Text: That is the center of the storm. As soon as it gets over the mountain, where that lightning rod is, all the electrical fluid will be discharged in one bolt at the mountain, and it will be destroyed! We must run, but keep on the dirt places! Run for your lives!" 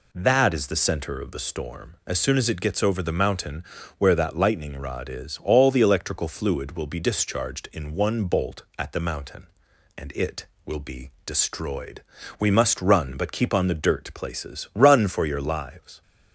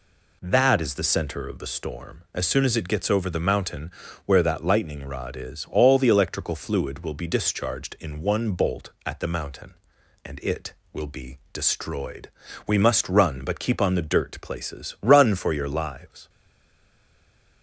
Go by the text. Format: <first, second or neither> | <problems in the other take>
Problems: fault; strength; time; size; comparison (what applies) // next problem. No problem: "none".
first | stays silent after the last word; noticeable; from 16.2 s on; 1.4 s long